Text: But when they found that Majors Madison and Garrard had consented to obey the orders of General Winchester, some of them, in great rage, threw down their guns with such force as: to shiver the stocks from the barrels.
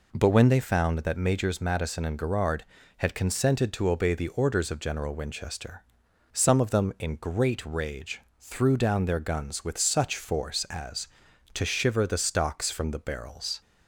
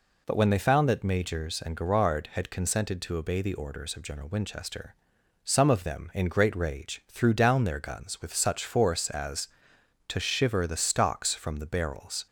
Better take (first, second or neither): first